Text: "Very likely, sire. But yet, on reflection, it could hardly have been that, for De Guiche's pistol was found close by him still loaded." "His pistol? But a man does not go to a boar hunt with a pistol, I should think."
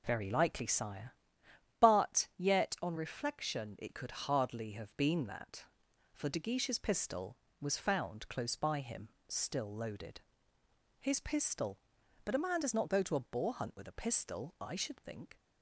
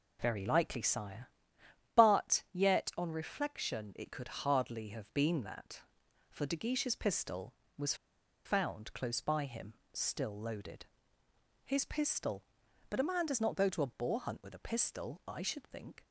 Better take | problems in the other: first | pauses between "was" and "found"; noticeable; at 7.9 s; 0.51 s long // pauses between "him" and "still"; slight; at 9.7 s; 0.22 s long; slight in the first

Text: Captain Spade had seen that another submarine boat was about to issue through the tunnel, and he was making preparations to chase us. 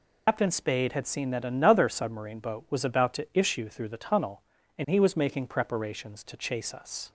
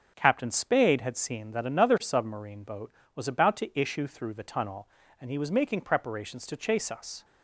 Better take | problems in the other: second | loses the start of "Captain"; at 0.2 s; 115 ms

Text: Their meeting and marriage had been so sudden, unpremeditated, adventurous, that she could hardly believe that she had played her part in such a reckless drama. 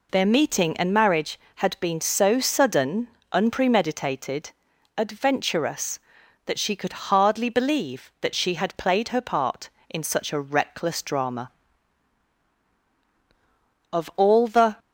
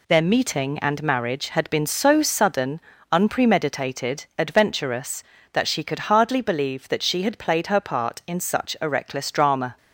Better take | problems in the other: second | goes on to say "Of all the"; noticeable; from 13.9 s on; 0.84 s long

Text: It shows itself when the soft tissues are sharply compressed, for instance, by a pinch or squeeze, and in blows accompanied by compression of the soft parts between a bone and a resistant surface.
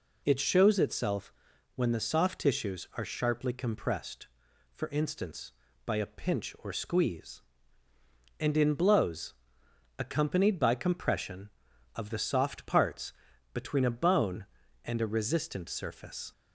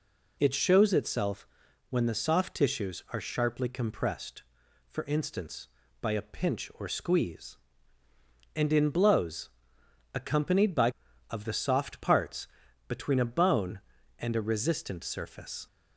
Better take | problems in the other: first | pauses between "itself" and "when"; at 1.4 s; 0.44 s long; also in the first // pauses between "blows" and "accompanied"; noticeable; at 9.4 s; 0.64 s long; noticeable in the first // skips "compression"; at 11.0 s // pauses between "parts" and "between"; at 12.4 s; 0.42 s long; also in the first

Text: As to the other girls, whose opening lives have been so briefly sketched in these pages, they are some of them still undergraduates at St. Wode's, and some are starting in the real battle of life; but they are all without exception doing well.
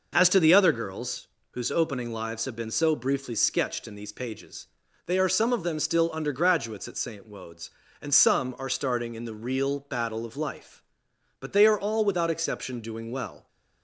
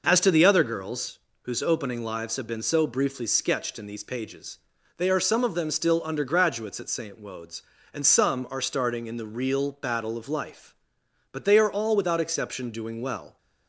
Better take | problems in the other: neither | none

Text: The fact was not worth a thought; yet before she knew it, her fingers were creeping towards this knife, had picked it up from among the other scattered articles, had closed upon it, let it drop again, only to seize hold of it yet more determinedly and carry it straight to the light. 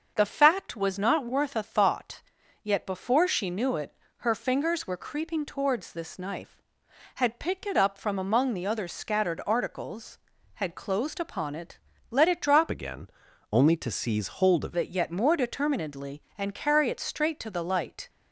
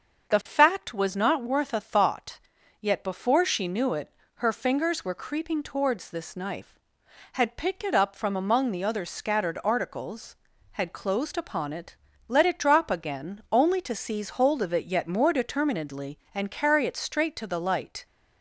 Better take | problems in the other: second | starts louder than the rest; until 1.1 s; 6.5 dB; also in the second // changes voice from "again" to "of"; from 12.6 to 14.7 s; 2.1 s long

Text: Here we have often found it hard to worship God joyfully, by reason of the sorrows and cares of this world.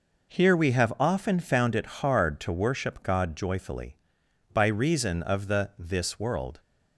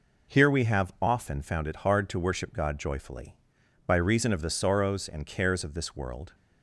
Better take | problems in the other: second | skips "sorrows and cares of"; at 5.7 s

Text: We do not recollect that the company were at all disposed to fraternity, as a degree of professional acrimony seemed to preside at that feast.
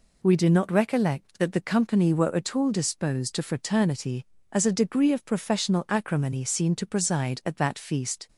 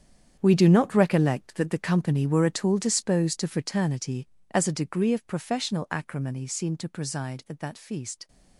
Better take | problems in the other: first | gets quieter; strong; throughout; 13 dB

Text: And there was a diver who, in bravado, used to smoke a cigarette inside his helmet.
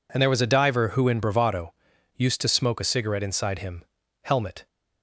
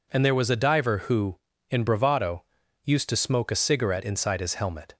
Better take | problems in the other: second | says "him" for "his"; at 3.5 s

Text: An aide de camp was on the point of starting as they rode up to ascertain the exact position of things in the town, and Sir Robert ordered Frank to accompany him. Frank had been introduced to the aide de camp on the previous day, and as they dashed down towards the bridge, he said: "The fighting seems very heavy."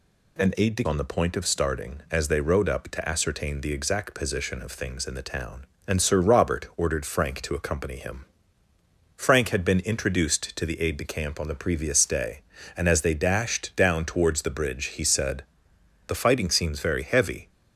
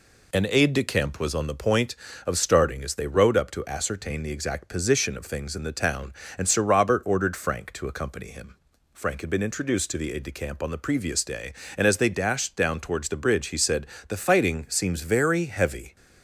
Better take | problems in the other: second | skips "camp was"; at 0.8 s

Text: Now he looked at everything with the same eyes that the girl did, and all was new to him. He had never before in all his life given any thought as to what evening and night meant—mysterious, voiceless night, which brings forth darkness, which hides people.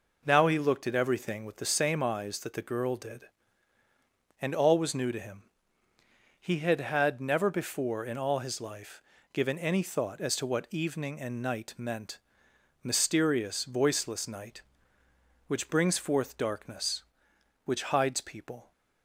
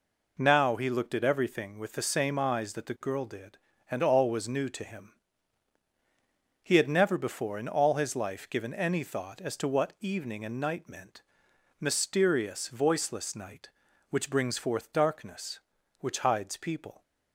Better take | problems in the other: second | says "had" twice; at 6.8 s // pauses between "life" and "given"; slight; at 9.0 s; 0.32 s long

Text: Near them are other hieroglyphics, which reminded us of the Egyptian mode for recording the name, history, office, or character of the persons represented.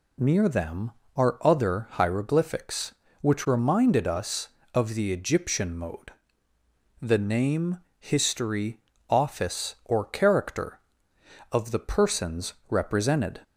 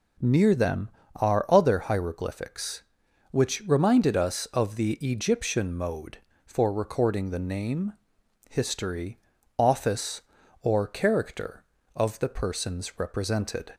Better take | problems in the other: second | skips "for recording"; at 6.5 s // pauses between "persons" and "represented"; slight; at 12.5 s; 0.16 s long

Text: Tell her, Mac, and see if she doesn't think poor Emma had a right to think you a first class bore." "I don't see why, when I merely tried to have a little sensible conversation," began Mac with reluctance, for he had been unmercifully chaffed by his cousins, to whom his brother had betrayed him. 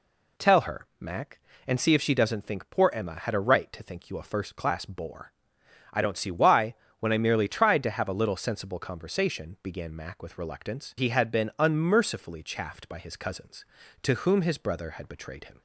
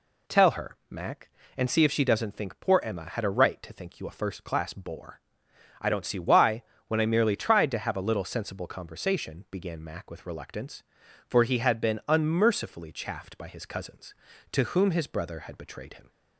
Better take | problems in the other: second | skips "for"; at 10.9 s

